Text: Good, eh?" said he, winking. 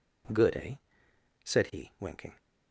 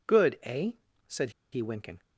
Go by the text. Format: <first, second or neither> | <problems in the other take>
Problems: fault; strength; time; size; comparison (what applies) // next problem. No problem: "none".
first | pauses between "said" and "he"; slight; at 1.2 s; 0.22 s long